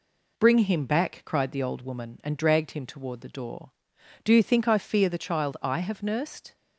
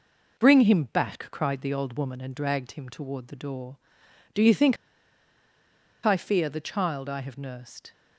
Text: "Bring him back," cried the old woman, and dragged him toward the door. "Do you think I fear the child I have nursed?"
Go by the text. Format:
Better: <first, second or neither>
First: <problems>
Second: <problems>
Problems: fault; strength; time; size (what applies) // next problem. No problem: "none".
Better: first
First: none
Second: pauses between "think" and "I"; strong; at 4.7 s; 1.2 s long